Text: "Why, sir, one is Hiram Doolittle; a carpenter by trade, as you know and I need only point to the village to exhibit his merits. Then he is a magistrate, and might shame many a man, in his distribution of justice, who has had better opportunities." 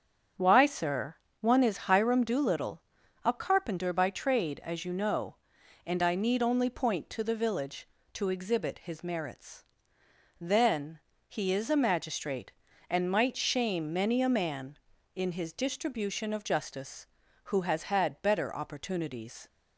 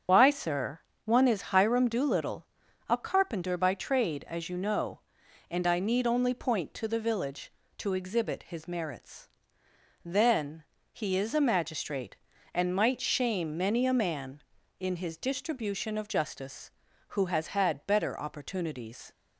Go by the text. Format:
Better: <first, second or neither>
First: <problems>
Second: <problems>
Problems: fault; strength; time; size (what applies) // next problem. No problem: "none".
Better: first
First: starts louder than the rest; strong; until 1.6 s; 7.5 dB // pauses between "Then" and "he"; slight; at 10.9 s; 0.30 s long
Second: loses the start of "Why"; at 0.0 s; 75 ms // starts louder than the rest; until 1.3 s; 7 dB // pauses between "Then" and "he"; slight; at 10.6 s; 0.30 s long